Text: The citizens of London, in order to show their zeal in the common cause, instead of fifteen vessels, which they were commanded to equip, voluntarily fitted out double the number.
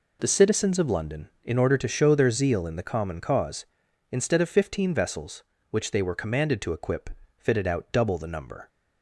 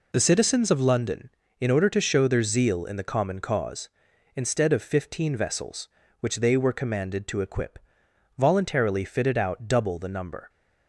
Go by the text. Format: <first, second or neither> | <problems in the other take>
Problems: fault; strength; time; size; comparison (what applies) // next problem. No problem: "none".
second | skips "voluntarily"; at 7.2 s